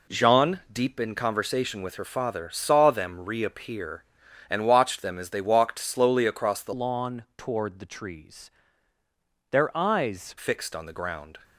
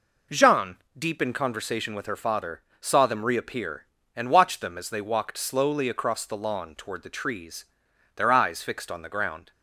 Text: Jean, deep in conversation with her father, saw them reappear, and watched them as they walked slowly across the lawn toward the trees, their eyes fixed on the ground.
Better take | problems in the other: second | changes voice from "lawn" to "eyes"; from 6.7 to 10.3 s; 3.6 s long

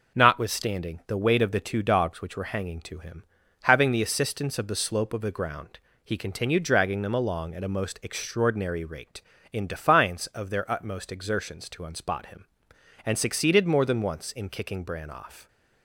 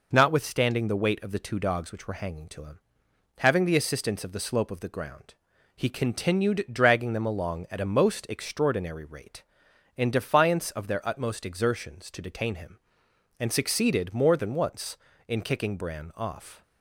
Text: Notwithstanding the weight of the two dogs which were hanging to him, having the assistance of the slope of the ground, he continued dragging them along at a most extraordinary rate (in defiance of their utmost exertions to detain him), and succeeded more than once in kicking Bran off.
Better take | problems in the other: second | says "unspot" for "detain"; at 11.8 s

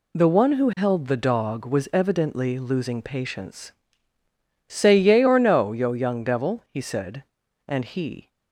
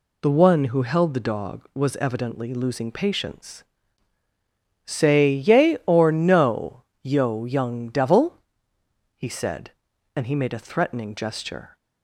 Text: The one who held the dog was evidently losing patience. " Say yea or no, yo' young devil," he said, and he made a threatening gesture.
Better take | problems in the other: second | stops before "made a threatening gesture"; at 8.2 s

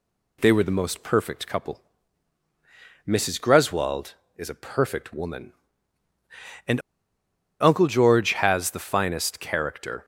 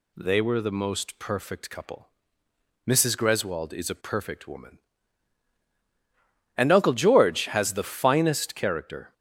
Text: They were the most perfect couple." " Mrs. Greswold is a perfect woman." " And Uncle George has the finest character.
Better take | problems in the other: second | pauses between "And" and "Uncle"; noticeable; at 6.7 s; 0.81 s long

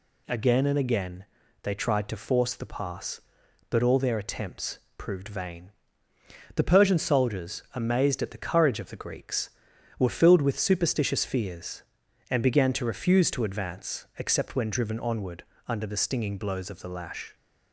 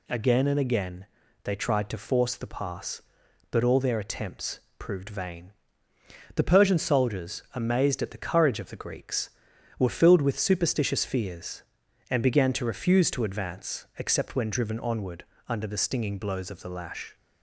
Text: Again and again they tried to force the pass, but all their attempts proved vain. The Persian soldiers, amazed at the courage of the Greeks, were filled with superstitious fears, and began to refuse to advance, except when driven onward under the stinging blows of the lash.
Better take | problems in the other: neither | pauses between "again" and "they"; the same in both // pauses between "attempts" and "proved"; slight; the same in both // pauses between "onward" and "under"; slight; the same in both

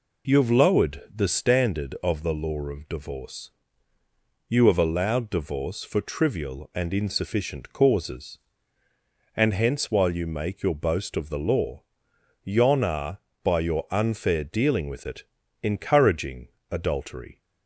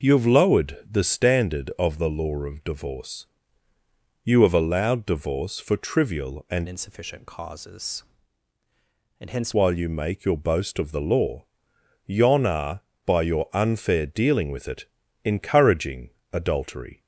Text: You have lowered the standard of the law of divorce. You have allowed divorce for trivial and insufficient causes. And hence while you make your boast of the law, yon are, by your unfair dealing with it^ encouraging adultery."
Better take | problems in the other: first | changes voice from "insufficient" to "hence"; from 6.6 to 9.5 s; 2.9 s long // pauses between "it" and "encouraging"; at 14.8 s; 0.40 s long; also in the first // pauses between "encouraging" and "adultery"; slight; at 16.1 s; 0.24 s long; slight in the first

